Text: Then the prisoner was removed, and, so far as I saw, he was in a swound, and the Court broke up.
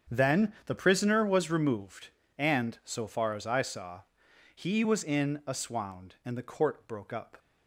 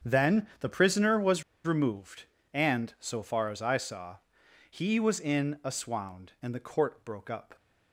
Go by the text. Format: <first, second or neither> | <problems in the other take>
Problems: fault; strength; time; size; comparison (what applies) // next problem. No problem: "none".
first | starts louder than the rest; strong; until 1.1 s; 8 dB; strong in the first // pauses between "was" and "removed"; slight; at 1.4 s; 0.22 s long